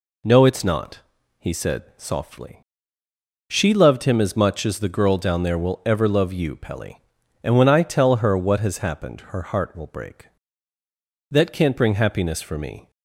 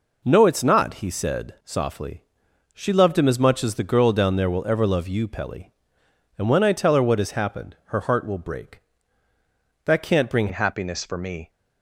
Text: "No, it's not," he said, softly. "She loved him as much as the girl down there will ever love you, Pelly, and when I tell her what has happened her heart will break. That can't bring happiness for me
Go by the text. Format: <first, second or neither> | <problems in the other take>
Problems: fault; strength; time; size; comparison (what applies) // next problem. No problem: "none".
first | changes voice at "happiness"; from 10.5 s on; 0.9 s long